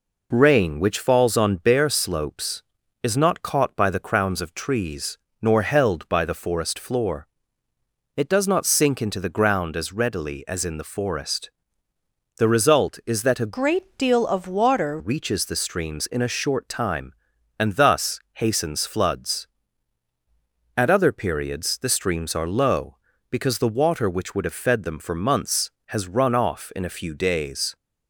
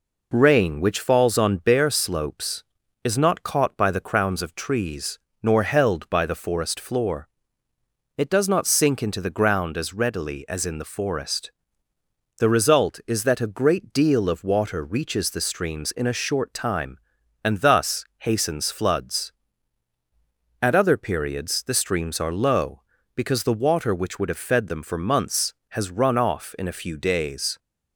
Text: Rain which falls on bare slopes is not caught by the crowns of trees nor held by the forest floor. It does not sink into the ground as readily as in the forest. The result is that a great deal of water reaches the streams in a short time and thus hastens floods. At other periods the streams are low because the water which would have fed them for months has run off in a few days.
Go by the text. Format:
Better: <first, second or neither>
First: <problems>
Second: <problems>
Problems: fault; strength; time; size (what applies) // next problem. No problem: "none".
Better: second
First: pauses between "trees" and "nor"; slight; at 5.1 s; 0.24 s long // changes voice from "great" to "water"; from 13.5 to 14.9 s; 1.4 s long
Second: pauses between "trees" and "nor"; slight; at 5.1 s; 0.24 s long